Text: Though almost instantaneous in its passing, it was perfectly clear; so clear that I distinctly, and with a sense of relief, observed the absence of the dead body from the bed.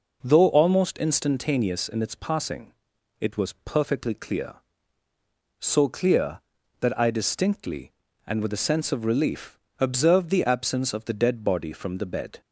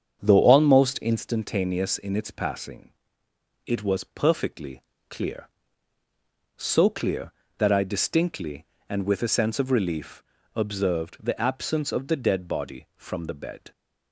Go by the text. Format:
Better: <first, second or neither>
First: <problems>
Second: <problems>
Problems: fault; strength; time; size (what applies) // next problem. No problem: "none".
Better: first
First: none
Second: starts louder than the rest; strong; until 1.3 s; 8 dB // pauses between "perfectly" and "clear"; slight; at 4.8 s; 0.28 s long